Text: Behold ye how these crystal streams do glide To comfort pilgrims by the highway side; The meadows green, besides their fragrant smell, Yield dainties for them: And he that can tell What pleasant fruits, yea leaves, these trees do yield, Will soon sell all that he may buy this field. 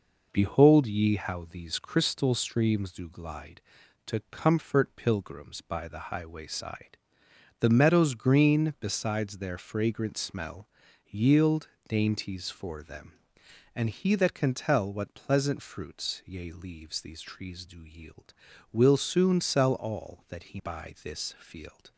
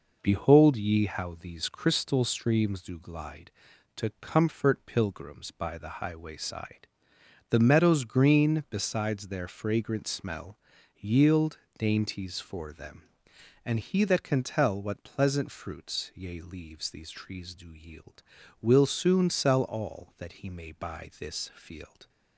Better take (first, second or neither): second